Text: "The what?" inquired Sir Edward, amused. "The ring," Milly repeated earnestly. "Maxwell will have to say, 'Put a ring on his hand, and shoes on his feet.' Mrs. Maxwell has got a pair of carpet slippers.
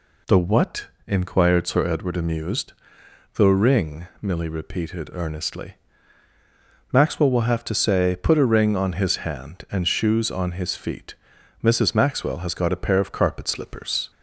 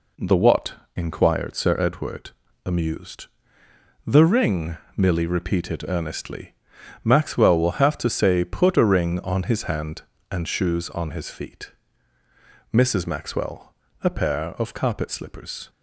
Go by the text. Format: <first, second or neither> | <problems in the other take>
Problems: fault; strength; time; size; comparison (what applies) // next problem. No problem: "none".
first | skips "has got"; at 13.8 s